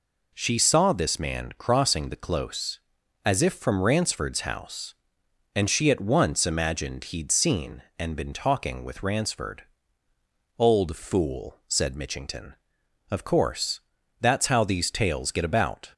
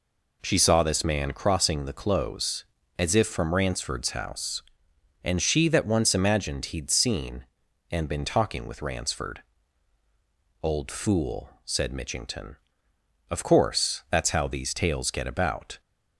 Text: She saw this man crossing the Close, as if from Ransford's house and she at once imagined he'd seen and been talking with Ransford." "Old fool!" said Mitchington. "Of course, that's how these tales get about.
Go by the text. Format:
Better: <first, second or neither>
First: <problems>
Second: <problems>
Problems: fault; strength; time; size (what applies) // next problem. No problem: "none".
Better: first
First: none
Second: says "that" for "at"; at 5.6 s